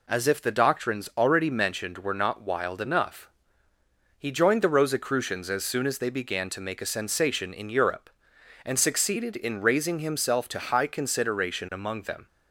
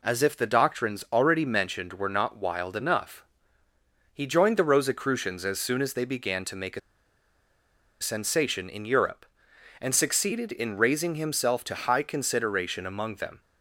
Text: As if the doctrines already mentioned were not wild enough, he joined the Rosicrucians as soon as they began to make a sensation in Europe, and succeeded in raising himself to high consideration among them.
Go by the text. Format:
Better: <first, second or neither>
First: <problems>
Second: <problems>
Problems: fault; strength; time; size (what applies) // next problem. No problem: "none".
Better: first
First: none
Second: pauses between "a" and "sensation"; at 6.7 s; 1.2 s long